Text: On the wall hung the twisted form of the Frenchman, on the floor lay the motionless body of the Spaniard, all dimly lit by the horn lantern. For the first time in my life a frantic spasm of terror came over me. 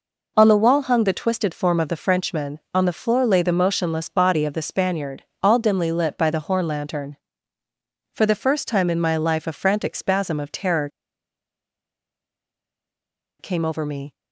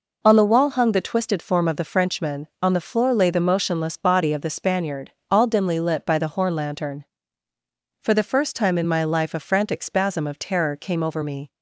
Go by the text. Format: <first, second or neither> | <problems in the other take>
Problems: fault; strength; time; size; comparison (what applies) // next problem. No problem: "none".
second | pauses between "terror" and "came"; strong; at 10.8 s; 2.5 s long